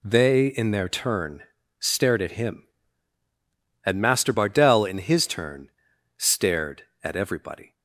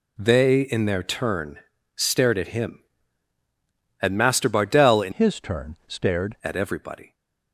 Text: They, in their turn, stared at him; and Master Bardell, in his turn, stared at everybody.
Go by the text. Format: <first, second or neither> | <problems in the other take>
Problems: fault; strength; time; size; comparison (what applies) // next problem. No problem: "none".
first | changes voice from "his" to "stared"; from 5.1 to 6.3 s; 1.2 s long